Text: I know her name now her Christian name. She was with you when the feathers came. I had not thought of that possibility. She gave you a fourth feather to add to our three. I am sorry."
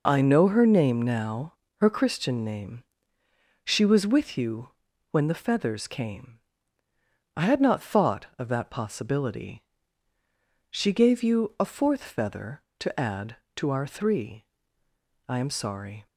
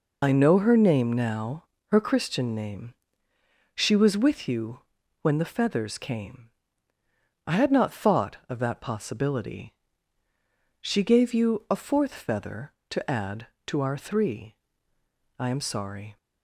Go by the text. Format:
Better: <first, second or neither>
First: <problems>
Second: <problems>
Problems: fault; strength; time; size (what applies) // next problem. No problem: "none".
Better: first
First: pauses between "now" and "her"; slight; at 1.5 s; 0.26 s long // pauses between "you" and "when"; at 4.6 s; 0.42 s long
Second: loses the start of "I"; at 0.2 s; 65 ms // pauses between "now" and "her"; slight; at 1.6 s; 0.26 s long // pauses between "you" and "when"; at 4.7 s; 0.42 s long